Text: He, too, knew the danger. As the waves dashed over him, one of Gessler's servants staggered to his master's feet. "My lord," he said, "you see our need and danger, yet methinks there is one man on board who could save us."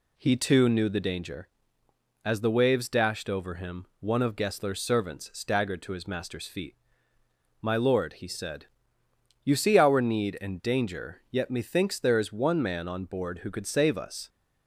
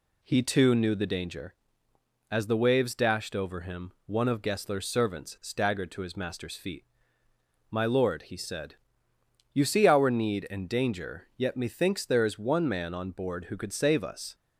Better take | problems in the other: neither | none

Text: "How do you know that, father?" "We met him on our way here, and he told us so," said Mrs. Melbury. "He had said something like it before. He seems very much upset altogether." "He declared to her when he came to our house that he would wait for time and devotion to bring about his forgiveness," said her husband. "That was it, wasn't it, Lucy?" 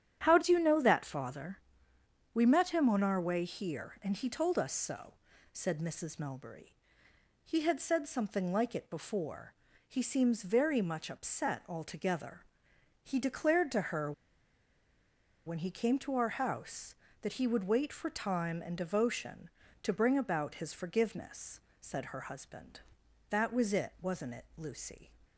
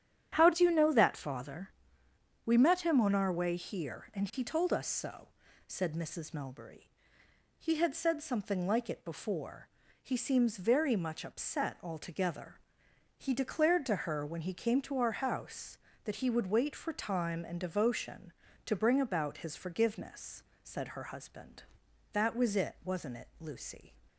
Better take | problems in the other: second | starts louder than the rest; strong; until 1.2 s; 10 dB; strong in the second // pauses between "her" and "when"; strong; at 14.1 s; 1.3 s long

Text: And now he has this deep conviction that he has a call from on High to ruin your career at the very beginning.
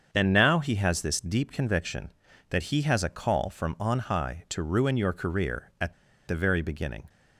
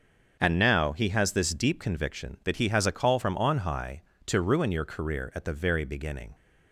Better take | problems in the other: second | starts louder than the rest; strong; until 1.1 s; 7 dB; also in the second // pauses between "at" and "the"; slight; at 5.9 s; 0.34 s long

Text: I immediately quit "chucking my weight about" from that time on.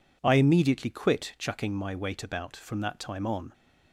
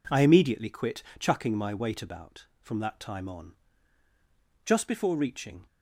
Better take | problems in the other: first | pauses between "quit" and "chucking"; slight; at 1.0 s; 0.16 s long // goes on to say "Just before reaching"; noticeable; from 4.6 s on; 1.0 s long

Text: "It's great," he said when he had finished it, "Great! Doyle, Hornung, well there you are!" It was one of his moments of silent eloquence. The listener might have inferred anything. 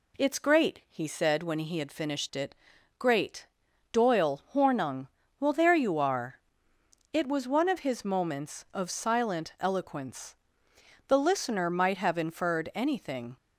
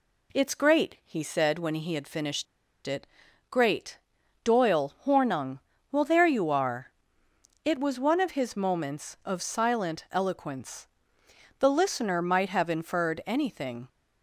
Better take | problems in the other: first | pauses between "finished" and "it"; at 2.4 s; 0.40 s long

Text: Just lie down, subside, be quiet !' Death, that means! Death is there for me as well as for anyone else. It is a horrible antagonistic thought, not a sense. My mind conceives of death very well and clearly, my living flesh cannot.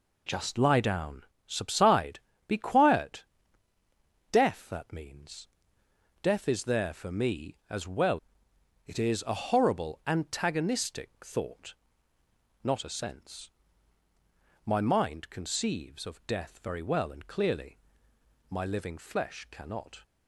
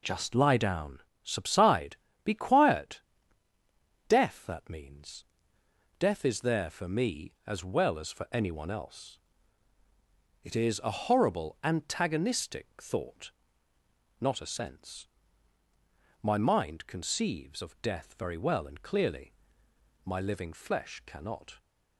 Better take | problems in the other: second | skips "as for anyone else"; at 8.5 s // pauses between "antagonistic" and "thought"; slight; at 11.0 s; 0.16 s long; slight in the second

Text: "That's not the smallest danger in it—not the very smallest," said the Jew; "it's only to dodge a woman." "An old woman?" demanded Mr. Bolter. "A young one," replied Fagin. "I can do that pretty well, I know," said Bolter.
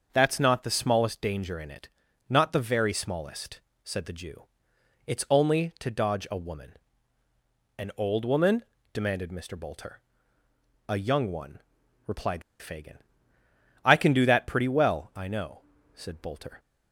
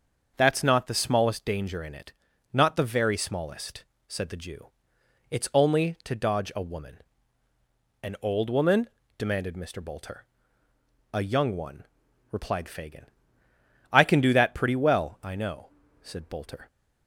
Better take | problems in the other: second | starts louder than the rest; until 1.1 s; 6.5 dB; also in the second // pauses between "replied" and "Fagin"; slight; at 12.4 s; 0.18 s long

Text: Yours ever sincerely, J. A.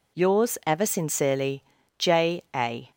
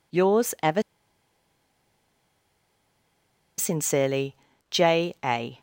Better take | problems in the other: first | pauses between "ever" and "sincerely"; strong; at 0.8 s; 2.7 s long

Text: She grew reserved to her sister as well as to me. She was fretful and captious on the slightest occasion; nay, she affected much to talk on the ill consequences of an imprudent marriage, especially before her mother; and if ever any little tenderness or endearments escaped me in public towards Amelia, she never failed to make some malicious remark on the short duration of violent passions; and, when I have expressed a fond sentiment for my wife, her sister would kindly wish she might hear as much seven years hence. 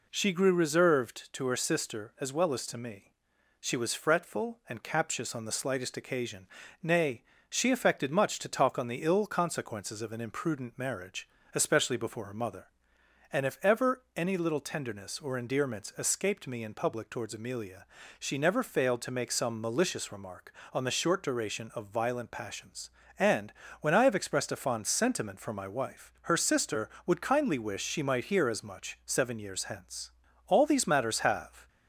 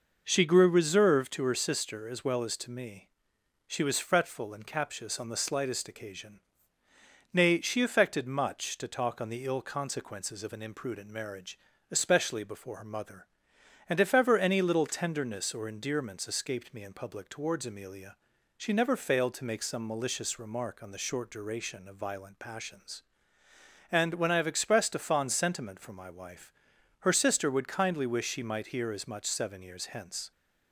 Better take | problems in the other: second | goes on to say "All these matters have"; noticeable; from 30.4 s on; 1.2 s long

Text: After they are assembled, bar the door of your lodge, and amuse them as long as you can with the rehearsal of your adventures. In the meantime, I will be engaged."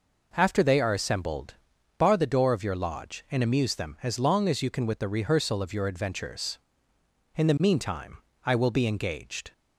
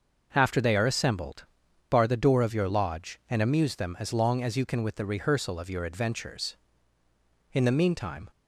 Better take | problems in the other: first | starts louder than the rest; noticeable; until 1.3 s; 6 dB // stops before "I will be engaged"; at 8.3 s

